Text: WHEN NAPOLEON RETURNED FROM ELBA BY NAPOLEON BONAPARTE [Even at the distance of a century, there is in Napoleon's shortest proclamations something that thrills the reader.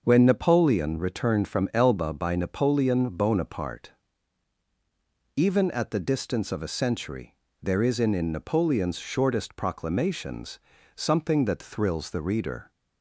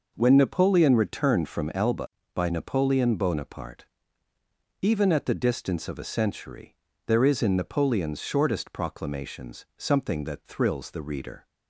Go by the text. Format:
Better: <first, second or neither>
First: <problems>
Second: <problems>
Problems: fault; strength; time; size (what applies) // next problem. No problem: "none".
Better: second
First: starts louder than the rest; until 1.0 s; 6.5 dB // pauses between "BONAPARTE" and "Even"; strong; at 3.9 s; 1.4 s long // says "in" twice; at 8.1 s // pauses between "proclamations" and "something"; slight; at 10.5 s; 0.36 s long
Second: pauses between "BONAPARTE" and "Even"; noticeable; at 3.8 s; 0.94 s long